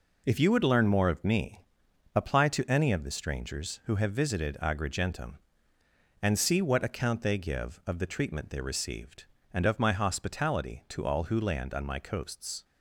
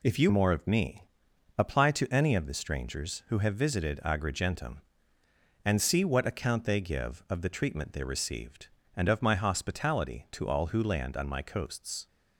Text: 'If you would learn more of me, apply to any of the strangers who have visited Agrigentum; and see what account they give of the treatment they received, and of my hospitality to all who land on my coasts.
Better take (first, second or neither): first